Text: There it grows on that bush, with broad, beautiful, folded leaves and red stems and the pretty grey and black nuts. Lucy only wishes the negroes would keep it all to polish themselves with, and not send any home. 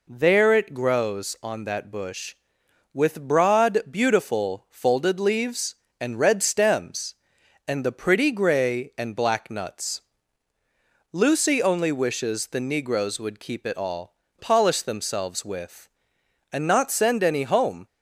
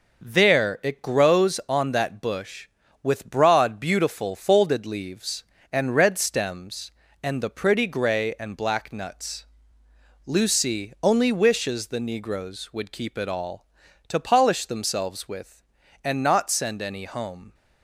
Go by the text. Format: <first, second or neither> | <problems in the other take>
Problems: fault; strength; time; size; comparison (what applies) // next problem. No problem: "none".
second | skips "to"; at 14.2 s